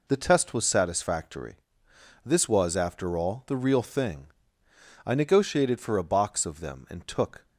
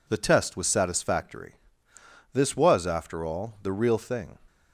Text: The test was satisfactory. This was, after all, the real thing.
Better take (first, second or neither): second